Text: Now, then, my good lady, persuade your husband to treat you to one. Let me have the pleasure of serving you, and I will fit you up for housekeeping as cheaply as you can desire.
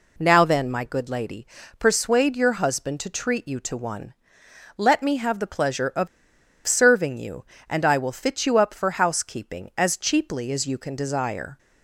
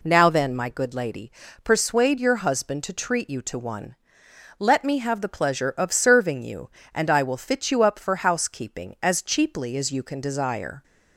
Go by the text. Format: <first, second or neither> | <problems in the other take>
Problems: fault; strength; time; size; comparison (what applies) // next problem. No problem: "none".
second | pauses between "of" and "serving"; noticeable; at 6.0 s; 0.59 s long